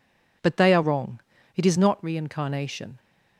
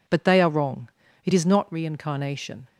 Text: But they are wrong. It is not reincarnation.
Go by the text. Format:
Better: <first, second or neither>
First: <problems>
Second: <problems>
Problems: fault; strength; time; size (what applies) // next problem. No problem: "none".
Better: neither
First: none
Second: none